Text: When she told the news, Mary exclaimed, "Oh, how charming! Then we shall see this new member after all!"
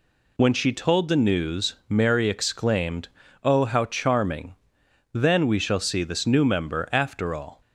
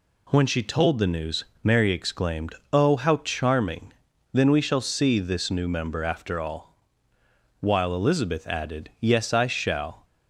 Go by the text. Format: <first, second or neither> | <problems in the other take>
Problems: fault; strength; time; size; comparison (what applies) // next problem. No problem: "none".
first | goes on to say "while Elizabeth added Yes I shall"; strong; from 7.6 s on; 2.4 s long